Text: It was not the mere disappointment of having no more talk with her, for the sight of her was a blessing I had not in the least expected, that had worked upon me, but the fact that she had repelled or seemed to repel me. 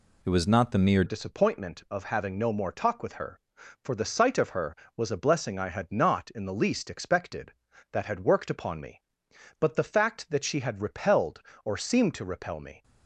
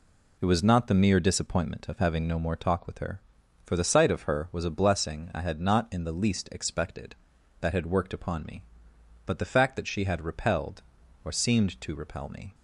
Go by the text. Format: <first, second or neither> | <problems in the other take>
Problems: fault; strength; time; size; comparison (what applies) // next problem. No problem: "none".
second | changes voice at "disappointment"; from 1.0 s on; 11.8 s long